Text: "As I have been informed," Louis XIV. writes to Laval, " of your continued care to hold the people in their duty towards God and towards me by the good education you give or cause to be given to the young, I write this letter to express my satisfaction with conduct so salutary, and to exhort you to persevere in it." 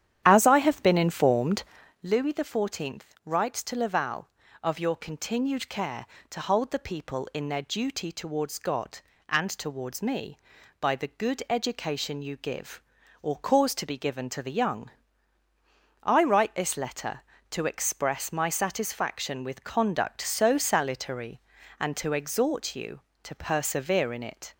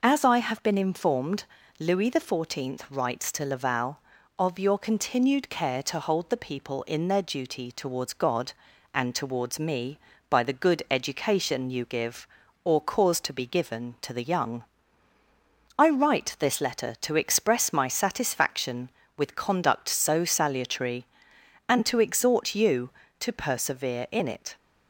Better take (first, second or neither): second